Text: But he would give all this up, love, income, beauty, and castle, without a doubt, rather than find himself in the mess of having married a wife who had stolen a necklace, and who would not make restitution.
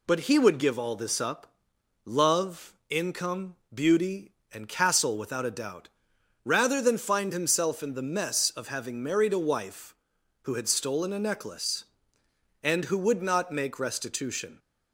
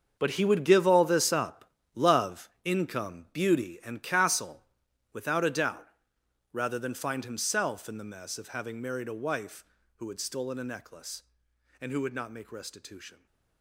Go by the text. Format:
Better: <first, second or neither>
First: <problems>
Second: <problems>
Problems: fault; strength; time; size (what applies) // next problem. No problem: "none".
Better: first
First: none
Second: gets quieter; strong; throughout; 14 dB